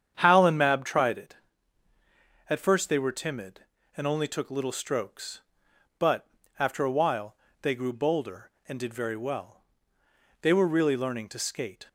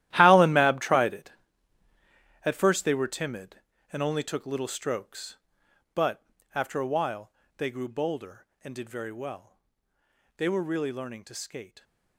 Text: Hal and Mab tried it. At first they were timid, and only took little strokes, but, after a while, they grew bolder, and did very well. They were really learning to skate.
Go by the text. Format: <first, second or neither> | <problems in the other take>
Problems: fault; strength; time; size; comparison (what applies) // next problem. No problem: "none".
first | gets quieter; strong; throughout; 16 dB // starts louder than the rest; strong; until 1.1 s; 14 dB; strong in the first